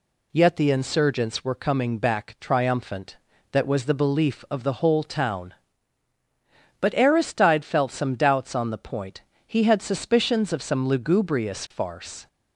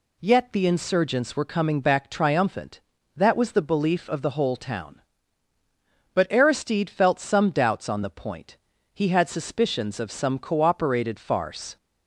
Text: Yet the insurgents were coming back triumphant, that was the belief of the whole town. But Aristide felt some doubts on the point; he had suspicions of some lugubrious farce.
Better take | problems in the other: first | says "cooperated" for "lugubrious"; at 10.3 s

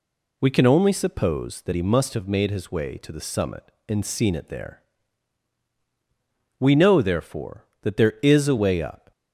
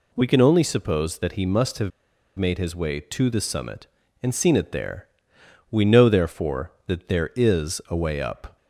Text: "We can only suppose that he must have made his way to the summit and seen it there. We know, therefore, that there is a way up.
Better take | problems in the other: first | pauses between "have" and "made"; noticeable; at 1.9 s; 0.47 s long

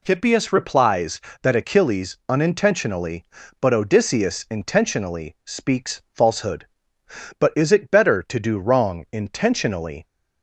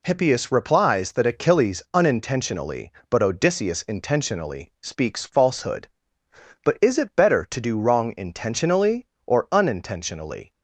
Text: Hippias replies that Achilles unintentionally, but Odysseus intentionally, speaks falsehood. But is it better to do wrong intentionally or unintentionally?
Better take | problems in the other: second | stops before "or unintentionally"; at 10.0 s

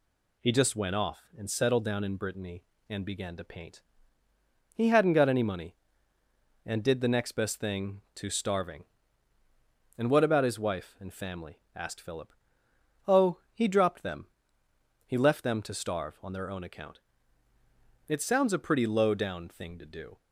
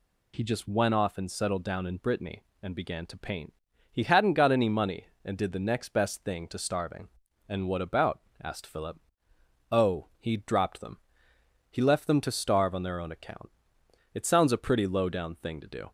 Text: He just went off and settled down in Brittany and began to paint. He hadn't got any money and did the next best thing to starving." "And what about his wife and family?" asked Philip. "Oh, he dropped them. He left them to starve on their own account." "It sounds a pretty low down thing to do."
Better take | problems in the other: first | skips "his wife and family"; at 8.3 s

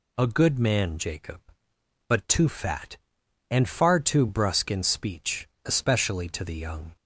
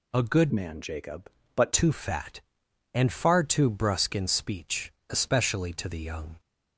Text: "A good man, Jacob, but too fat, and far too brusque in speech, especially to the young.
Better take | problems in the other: first | changes voice from "man" to "but"; from 0.5 to 1.7 s; 1.2 s long

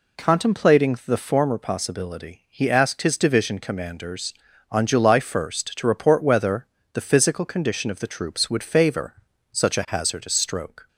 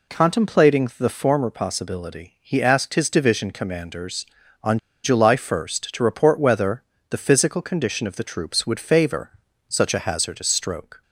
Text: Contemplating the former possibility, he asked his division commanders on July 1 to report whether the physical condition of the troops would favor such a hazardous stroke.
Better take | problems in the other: first | pauses between "on" and "July"; slight; at 4.7 s; 0.26 s long // pauses between "whether" and "the"; slight; at 6.8 s; 0.28 s long; slight in the first // pauses between "favor" and "such"; slight; at 9.3 s; 0.36 s long; slight in the first

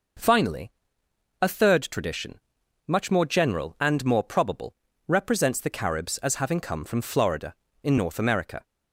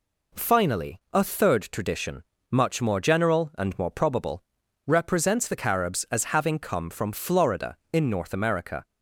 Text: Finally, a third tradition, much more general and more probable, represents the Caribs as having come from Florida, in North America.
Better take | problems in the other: neither | none

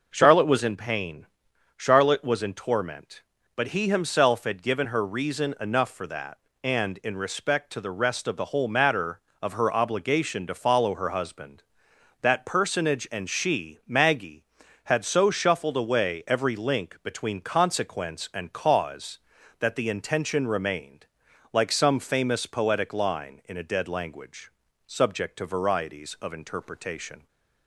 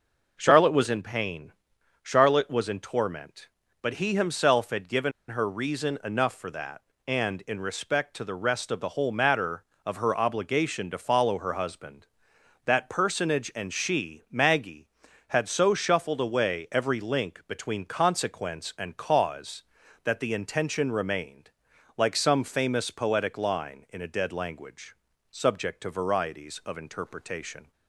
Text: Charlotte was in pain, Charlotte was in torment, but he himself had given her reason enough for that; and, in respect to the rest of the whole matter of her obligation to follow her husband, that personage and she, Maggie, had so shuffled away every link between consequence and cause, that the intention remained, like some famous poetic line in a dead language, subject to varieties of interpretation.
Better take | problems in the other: first | pauses between "given" and "her"; slight; at 5.1 s; 0.18 s long

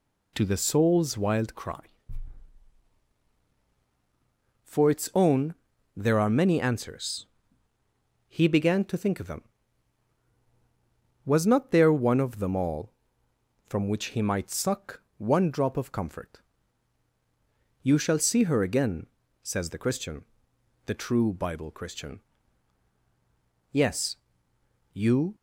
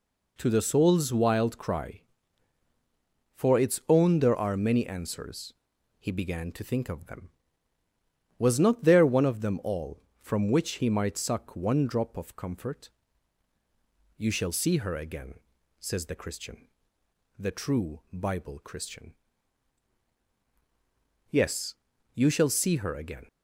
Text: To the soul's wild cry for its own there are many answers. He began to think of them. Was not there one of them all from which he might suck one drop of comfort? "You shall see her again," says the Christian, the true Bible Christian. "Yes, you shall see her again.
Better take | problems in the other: second | pauses between "own" and "there"; at 5.5 s; 0.42 s long // pauses between "suck" and "one"; slight; at 15.0 s; 0.16 s long // stops before "shall see her again"; at 25.3 s

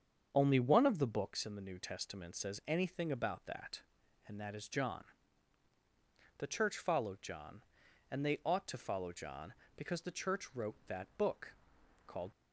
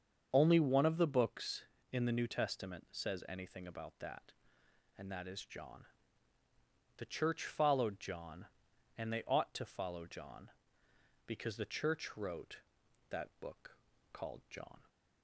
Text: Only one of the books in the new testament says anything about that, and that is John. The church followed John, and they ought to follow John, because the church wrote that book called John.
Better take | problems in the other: second | starts louder than the rest; until 1.3 s; 7 dB; also in the second // pauses between "book" and "called"; noticeable; at 11.5 s; 0.52 s long; slight in the second // stops before "John"; at 12.3 s

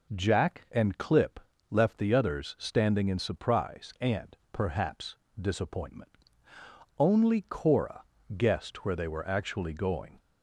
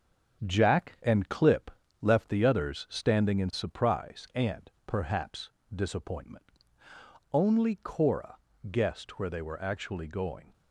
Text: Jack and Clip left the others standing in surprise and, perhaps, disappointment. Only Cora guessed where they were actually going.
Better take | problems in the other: first | gets quieter; noticeable; throughout; 6 dB // pauses between "Clip" and "left"; slight; at 1.7 s; 0.32 s long; slight in the first // pauses between "Cora" and "guessed"; slight; at 8.3 s; 0.34 s long; slight in the first

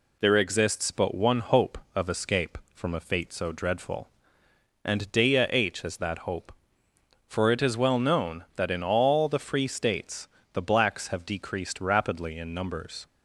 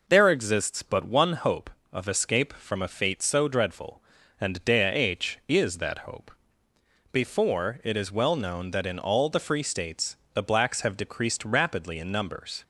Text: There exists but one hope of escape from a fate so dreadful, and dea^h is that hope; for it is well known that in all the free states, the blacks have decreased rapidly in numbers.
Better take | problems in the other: first | says "before" for "for"; at 7.1 s

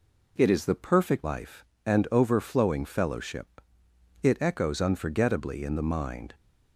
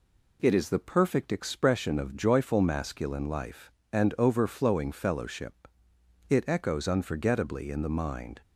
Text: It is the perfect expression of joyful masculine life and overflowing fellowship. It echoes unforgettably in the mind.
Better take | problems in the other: second | skips "expression of joyful masculine"; at 1.2 s

